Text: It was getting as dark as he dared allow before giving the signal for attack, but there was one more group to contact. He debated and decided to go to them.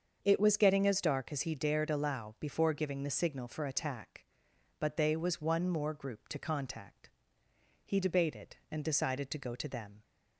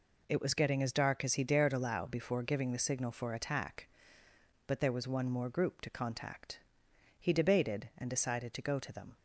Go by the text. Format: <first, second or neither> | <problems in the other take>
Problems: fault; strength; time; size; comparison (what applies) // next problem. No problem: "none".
second | starts louder than the rest; until 1.2 s; 7 dB // says "they" for "there"; at 4.9 s